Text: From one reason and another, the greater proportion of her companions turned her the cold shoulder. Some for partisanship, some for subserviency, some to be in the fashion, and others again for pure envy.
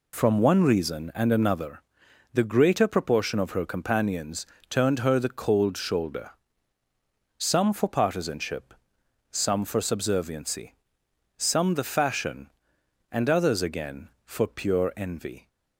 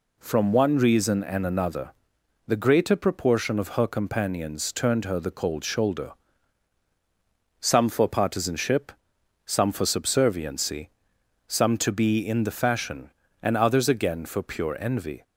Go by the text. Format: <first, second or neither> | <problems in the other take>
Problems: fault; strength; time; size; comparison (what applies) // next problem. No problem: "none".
second | pauses between "companions" and "turned"; slight; at 4.4 s; 0.24 s long // skips "to be in"; at 11.7 s